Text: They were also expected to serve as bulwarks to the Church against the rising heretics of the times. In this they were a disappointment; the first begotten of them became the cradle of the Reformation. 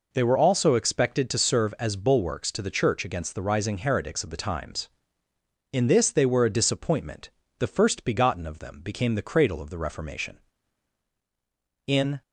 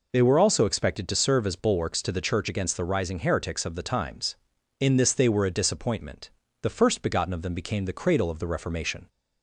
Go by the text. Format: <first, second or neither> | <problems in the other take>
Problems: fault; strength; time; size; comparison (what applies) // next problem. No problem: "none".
second | goes on to say "In"; slight; from 11.8 s on; 0.36 s long